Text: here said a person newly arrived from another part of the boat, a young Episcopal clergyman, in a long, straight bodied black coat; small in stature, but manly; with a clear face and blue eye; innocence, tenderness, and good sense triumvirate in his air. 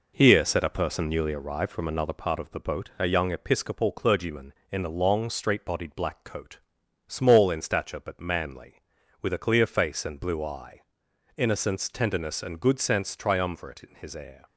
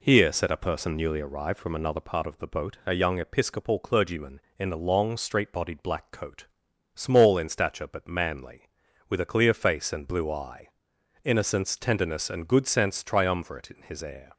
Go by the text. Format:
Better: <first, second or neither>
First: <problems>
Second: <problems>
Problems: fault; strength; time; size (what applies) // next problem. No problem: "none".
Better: second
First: gets quieter; noticeable; throughout; 5 dB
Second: none